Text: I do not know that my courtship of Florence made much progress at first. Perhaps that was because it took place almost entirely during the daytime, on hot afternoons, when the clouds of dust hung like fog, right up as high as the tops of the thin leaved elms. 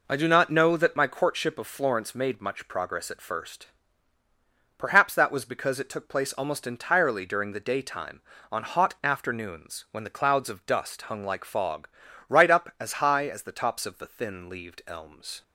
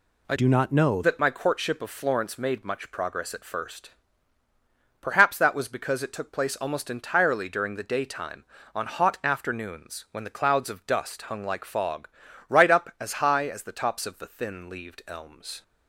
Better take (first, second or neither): first